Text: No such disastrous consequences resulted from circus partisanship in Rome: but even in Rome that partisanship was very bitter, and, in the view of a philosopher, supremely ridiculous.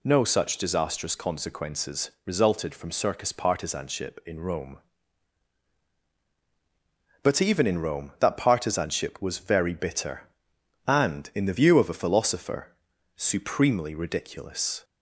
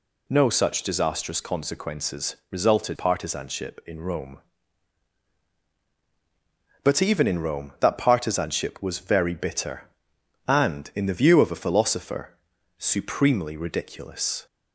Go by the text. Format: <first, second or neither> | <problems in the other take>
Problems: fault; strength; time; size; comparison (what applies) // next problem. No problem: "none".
first | skips "from circus"; at 2.9 s